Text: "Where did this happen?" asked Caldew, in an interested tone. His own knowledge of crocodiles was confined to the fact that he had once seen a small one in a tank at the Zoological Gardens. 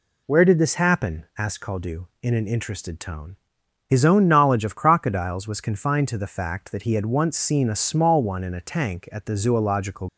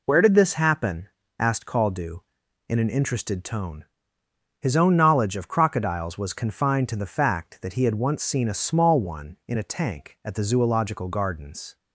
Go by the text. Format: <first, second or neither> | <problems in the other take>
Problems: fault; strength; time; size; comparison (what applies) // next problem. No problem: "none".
second | stops before "Gardens"; at 10.0 s